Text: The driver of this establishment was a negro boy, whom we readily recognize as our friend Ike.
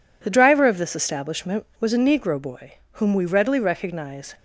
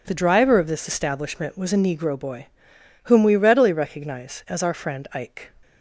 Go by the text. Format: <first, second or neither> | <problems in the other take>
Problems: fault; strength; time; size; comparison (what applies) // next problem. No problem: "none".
second | stops before "as our friend Ike"; at 4.3 s